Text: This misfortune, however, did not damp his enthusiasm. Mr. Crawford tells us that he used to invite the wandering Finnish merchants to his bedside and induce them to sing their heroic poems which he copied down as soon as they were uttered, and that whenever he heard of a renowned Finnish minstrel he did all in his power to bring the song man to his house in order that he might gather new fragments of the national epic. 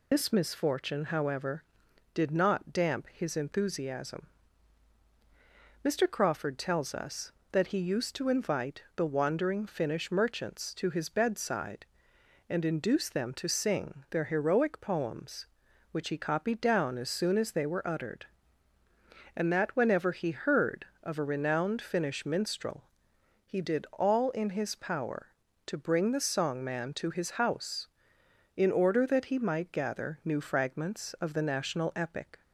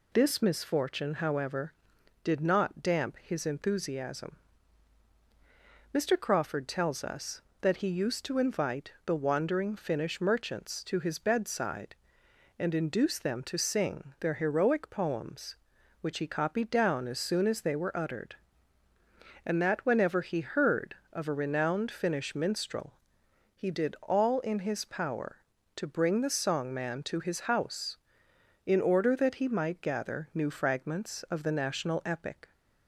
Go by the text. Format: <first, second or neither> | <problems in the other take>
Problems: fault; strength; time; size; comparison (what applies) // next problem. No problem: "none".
second | loses the start of "This"; at 0.1 s; 75 ms // pauses between "minstrel" and "he"; noticeable; at 22.8 s; 0.60 s long; noticeable in the second